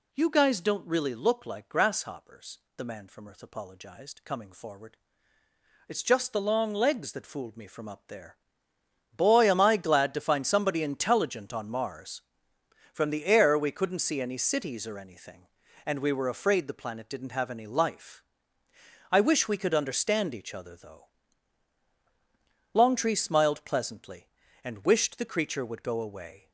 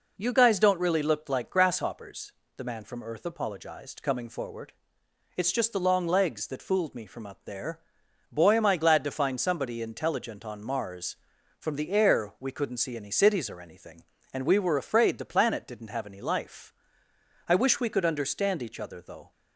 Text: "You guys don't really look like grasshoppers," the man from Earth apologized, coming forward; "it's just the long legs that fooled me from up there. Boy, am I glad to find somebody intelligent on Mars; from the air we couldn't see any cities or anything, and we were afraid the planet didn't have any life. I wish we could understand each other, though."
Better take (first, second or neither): second